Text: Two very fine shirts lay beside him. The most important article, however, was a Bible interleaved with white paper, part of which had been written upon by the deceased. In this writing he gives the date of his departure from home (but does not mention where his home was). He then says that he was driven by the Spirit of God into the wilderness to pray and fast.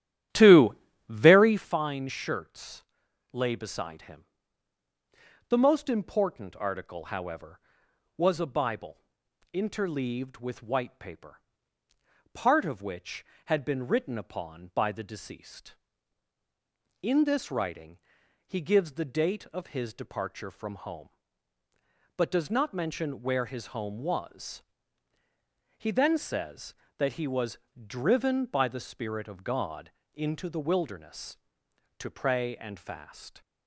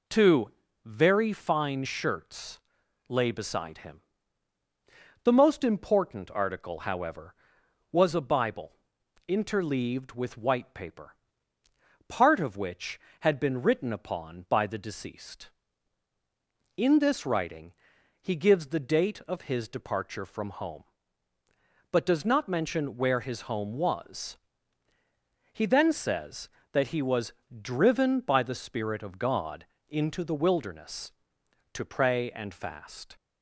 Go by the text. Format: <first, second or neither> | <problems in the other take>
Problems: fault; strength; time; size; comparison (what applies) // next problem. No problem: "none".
second | starts louder than the rest; strong; until 1.7 s; 12 dB // pauses between "Two" and "very"; slight; at 0.7 s; 0.34 s long; slight in the second // pauses between "shirts" and "lay"; noticeable; at 2.8 s; 0.50 s long; noticeable in the second // pauses between "Bible" and "interleaved"; noticeable; at 8.9 s; 0.54 s long; noticeable in the second // pauses between "writing" and "he"; noticeable; at 17.9 s; 0.48 s long; noticeable in the second // pauses between "was" and "driven"; slight; at 27.5 s; 0.30 s long; slight in the second // pauses between "God" and "into"; slight; at 29.9 s; 0.22 s long; slight in the second